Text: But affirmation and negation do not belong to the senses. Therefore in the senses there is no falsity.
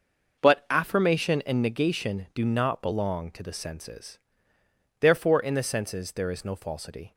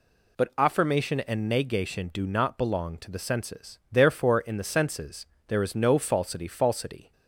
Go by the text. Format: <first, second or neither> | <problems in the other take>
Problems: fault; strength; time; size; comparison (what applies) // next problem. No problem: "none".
first | pauses between "senses" and "there"; slight; at 5.2 s; 0.22 s long // says "falsity" twice; at 6.4 s